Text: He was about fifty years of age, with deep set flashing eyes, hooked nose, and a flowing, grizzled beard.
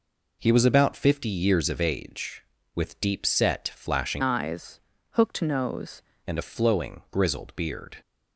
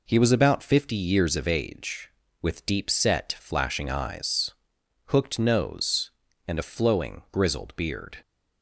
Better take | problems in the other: second | changes voice from "eyes" to "nose"; from 4.2 to 6.0 s; 1.8 s long

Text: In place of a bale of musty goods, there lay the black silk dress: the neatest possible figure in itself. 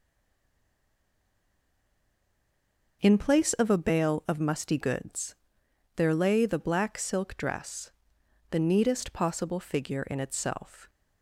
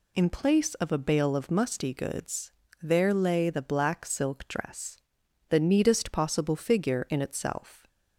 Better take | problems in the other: second | stays silent before the first word; strong; until 3.0 s; 3.0 s long

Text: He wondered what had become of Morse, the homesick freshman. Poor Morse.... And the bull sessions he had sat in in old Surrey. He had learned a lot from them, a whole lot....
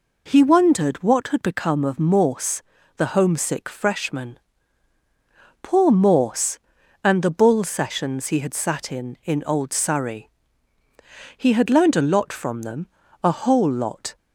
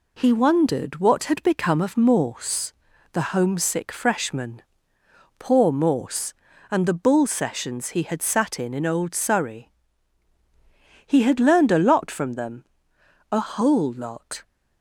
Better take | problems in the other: neither | none

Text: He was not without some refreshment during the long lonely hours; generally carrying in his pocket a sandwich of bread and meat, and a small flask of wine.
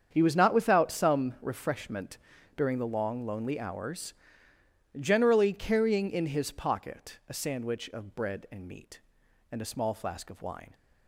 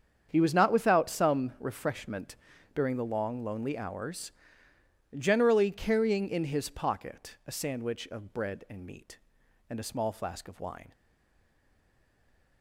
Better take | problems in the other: first | starts louder than the rest; strong; until 1.3 s; 7.5 dB; strong in the first // pauses between "refreshment" and "during"; at 2.3 s; 0.40 s long; also in the first // stays silent after the last word; noticeable; from 10.9 s on; 1.7 s long

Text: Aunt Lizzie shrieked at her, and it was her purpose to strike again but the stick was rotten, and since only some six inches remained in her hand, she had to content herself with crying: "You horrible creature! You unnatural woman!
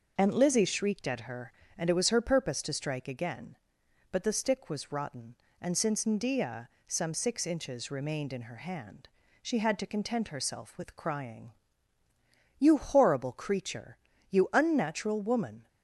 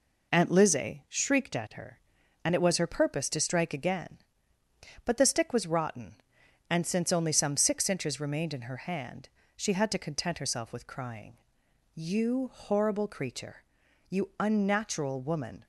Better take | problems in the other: second | says "ndia" for "only"; at 6.0 s

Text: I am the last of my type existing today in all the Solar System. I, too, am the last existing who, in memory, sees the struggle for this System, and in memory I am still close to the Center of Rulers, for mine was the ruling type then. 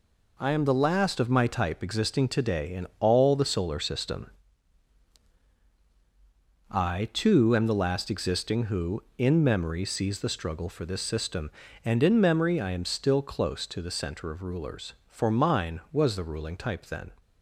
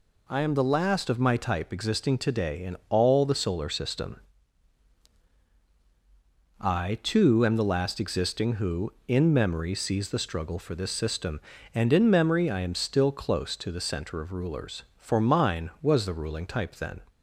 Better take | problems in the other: second | gets quieter; strong; throughout; 7.5 dB

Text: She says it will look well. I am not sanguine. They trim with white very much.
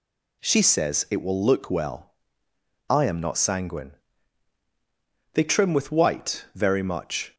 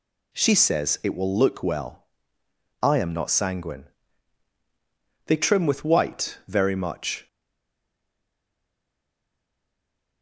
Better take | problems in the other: first | stays silent after the last word; strong; from 7.2 s on; 3.0 s long

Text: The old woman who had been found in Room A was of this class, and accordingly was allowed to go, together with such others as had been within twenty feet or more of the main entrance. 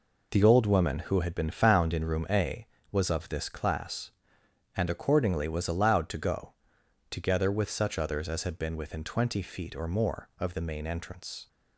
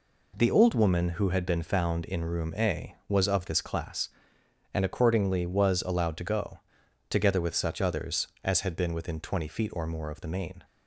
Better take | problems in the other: first | stops before "entrance"; at 10.6 s

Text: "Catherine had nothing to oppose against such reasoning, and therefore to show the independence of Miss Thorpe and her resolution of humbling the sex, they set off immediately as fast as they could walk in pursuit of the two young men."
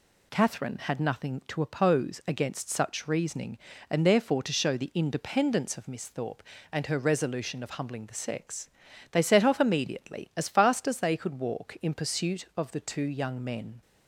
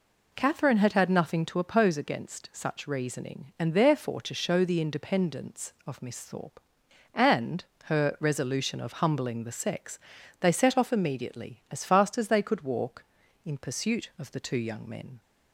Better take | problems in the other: first | says "had" twice; at 0.9 s // pauses between "and" and "her"; slight; at 7.6 s; 0.18 s long

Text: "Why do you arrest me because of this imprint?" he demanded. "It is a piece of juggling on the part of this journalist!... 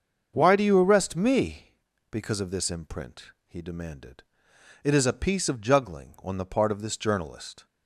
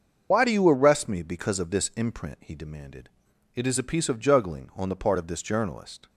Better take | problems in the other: first | loses the start of "Why"; at 0.3 s; 70 ms // starts louder than the rest; noticeable; until 1.3 s; 6 dB; also in the first

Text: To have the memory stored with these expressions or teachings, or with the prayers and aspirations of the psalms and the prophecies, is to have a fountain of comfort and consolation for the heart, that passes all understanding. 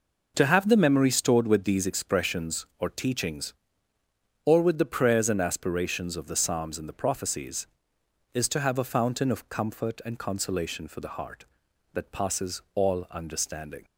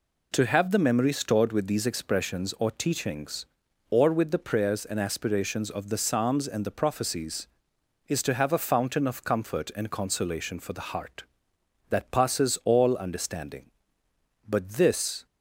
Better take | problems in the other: first | goes on to say "But this"; noticeable; from 14.4 s on; 0.78 s long

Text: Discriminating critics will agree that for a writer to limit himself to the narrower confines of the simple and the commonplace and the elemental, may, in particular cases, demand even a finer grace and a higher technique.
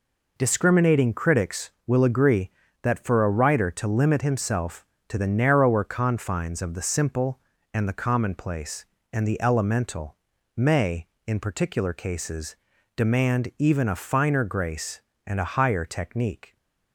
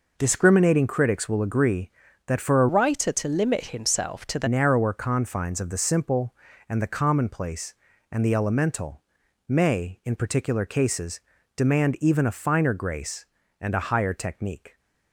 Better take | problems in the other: first | changes voice from "writer" to "the"; from 2.6 to 4.4 s; 1.8 s long

